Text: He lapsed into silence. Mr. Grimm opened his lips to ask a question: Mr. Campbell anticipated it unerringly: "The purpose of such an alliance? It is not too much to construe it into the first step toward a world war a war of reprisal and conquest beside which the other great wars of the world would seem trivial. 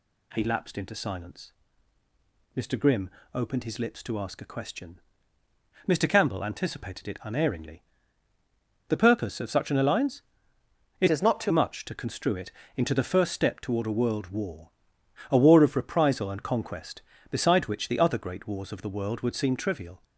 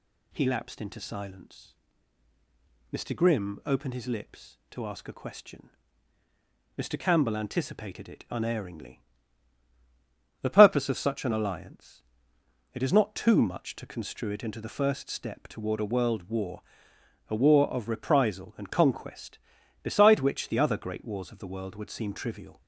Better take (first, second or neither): second